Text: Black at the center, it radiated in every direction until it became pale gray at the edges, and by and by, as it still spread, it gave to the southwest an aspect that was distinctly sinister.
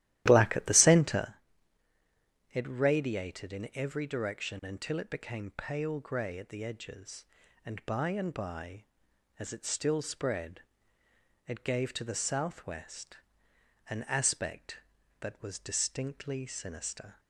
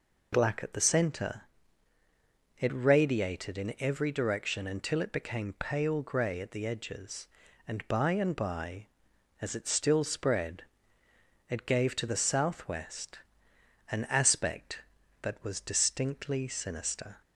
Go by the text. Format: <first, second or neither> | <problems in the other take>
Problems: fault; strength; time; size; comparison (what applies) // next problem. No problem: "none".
second | starts louder than the rest; strong; until 1.3 s; 14 dB // pauses between "southwest" and "an"; noticeable; at 13.1 s; 0.72 s long; noticeable in the second